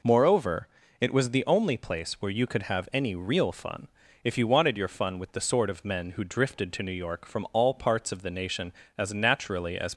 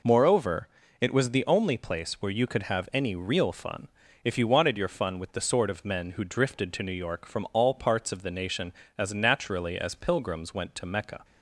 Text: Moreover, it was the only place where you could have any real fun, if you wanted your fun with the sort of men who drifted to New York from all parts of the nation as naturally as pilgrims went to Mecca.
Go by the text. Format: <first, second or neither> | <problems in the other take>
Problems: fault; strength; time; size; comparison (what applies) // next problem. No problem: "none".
second | stops before "pilgrims went to Mecca"; at 9.9 s